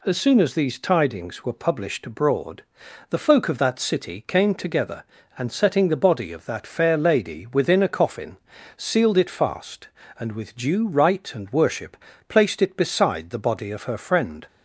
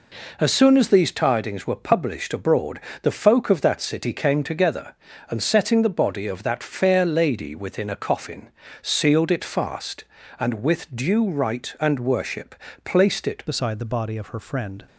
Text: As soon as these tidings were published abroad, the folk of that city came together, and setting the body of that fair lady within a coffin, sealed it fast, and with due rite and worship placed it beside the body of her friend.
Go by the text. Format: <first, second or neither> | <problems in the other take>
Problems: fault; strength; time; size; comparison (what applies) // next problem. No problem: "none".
first | pauses between "worship" and "placed"; slight; at 12.5 s; 0.30 s long; slight in the first // changes voice at "beside"; from 13.4 s on; 1.4 s long